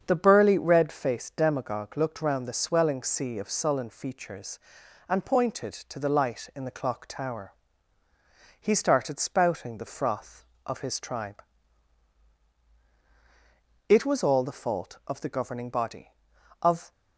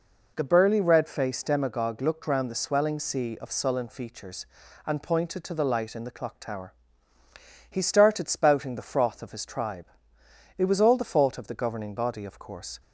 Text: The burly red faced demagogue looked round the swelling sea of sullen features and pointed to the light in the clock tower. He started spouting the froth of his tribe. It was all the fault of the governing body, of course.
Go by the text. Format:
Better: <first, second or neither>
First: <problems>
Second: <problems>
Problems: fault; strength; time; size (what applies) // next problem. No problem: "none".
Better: second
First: starts louder than the rest; strong; until 1.0 s; 7.5 dB // stops before "course"; at 16.9 s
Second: none